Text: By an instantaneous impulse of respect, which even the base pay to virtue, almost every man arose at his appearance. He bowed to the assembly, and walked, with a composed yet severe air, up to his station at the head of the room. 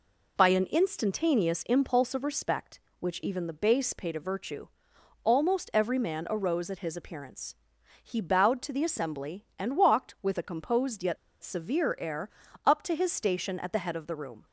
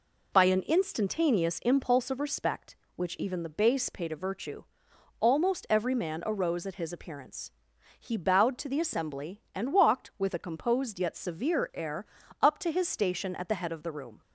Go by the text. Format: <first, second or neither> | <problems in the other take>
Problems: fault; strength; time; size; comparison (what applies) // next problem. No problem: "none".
second | pauses between "yet" and "severe"; slight; at 11.1 s; 0.26 s long